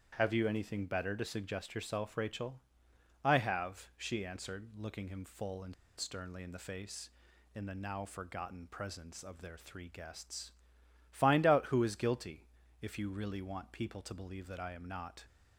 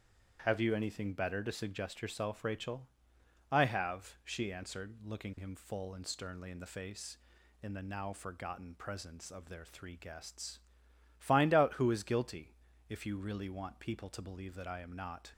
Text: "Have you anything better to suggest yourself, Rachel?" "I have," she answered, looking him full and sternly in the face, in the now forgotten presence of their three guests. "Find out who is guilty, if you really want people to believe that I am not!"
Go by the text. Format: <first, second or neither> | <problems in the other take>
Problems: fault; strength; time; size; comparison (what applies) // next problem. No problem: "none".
second | starts louder than the rest; strong; until 1.1 s; 9 dB; strong in the second // pauses between "and" and "sternly"; slight; at 5.7 s; 0.24 s long